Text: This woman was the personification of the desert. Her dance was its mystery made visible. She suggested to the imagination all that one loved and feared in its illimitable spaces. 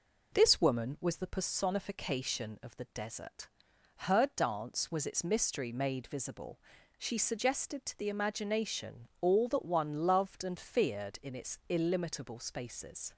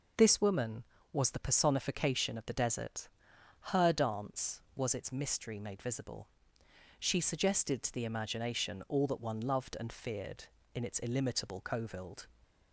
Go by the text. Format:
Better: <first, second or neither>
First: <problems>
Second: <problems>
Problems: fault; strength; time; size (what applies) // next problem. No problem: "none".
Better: first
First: none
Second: says "covild" for "spaces"; at 11.5 s